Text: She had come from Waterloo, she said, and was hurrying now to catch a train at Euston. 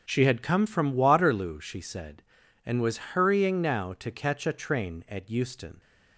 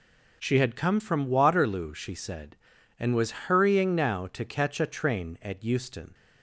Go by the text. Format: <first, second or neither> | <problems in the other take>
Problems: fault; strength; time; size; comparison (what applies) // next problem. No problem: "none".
second | starts louder than the rest; until 1.5 s; 6.5 dB